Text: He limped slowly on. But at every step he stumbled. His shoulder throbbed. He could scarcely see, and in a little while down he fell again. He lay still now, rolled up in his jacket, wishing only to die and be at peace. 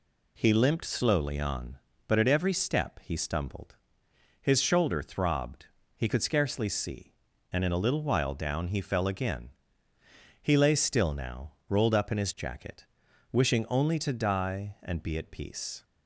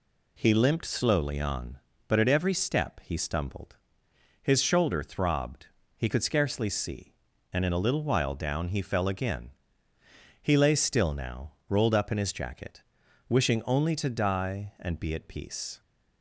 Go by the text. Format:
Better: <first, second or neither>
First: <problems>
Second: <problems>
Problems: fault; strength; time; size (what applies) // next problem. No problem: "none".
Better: neither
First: none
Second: none